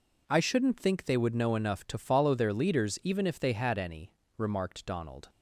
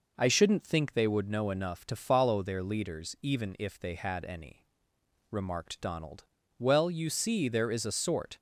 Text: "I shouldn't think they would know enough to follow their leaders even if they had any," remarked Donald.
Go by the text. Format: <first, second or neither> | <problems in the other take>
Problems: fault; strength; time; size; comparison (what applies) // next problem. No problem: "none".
first | goes on to say "Well you see there is a sort"; strong; from 6.5 s on; 1.7 s long